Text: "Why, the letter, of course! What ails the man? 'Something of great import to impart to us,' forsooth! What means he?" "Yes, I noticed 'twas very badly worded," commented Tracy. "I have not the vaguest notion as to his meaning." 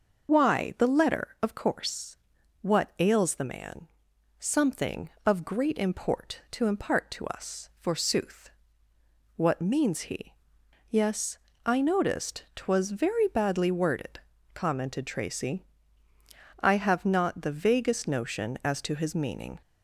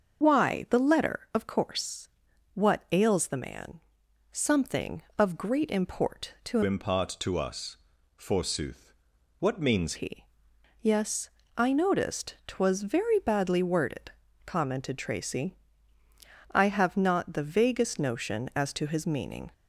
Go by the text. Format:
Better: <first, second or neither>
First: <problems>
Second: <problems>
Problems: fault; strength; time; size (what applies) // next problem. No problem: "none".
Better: first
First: none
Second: starts louder than the rest; until 1.2 s; 6.5 dB // changes voice from "impart" to "means"; from 6.6 to 9.9 s; 3.3 s long